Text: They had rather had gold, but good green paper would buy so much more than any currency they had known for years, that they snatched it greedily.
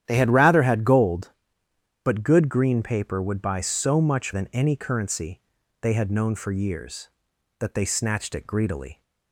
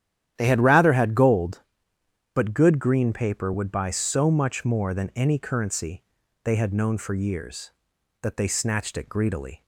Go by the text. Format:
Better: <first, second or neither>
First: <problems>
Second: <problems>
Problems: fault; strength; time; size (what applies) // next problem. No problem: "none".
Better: second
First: starts louder than the rest; strong; until 1.0 s; 10.5 dB // skips "more"; at 4.3 s // pauses between "currency" and "they"; at 5.4 s; 0.40 s long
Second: starts louder than the rest; strong; until 1.3 s; 10.5 dB // pauses between "currency" and "they"; at 6.0 s; 0.40 s long